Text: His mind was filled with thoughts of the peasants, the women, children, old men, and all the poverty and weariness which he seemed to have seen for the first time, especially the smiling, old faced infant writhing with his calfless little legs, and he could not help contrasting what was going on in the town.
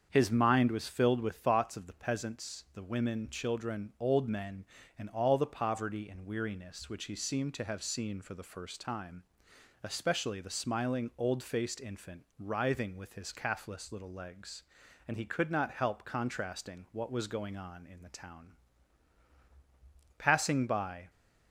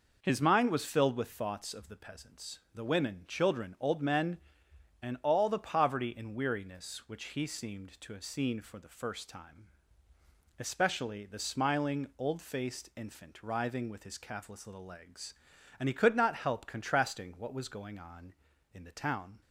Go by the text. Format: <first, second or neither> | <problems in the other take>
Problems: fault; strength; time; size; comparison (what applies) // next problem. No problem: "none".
second | starts louder than the rest; strong; until 1.1 s; 7 dB // pauses between "infant" and "writhing"; slight; at 12.2 s; 0.18 s long // goes on to say "Passing by"; noticeable; from 20.1 s on; 0.92 s long